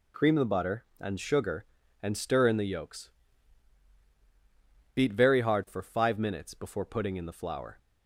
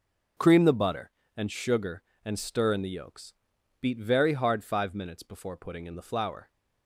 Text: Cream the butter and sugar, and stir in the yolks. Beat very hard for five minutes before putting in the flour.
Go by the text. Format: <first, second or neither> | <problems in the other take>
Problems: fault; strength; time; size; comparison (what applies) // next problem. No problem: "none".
first | starts louder than the rest; until 1.6 s; 6 dB // skips "for"; at 4.6 s